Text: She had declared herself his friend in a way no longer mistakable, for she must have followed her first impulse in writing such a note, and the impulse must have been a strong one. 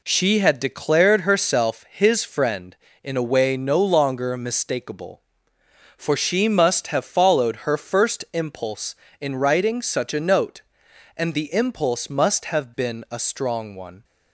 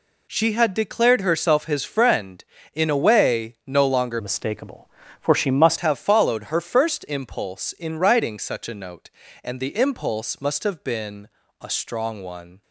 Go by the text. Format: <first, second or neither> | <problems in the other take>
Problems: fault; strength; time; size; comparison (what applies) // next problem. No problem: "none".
first | changes voice from "mistakable" to "must"; from 4.1 to 5.7 s; 1.6 s long // pauses between "been" and "a"; slight; at 11.2 s; 0.32 s long